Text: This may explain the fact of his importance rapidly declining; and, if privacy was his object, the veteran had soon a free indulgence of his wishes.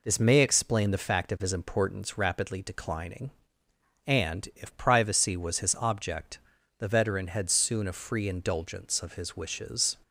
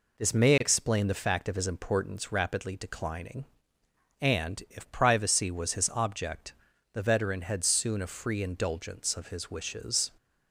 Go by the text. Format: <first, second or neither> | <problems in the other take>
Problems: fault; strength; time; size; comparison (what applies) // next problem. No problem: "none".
neither | none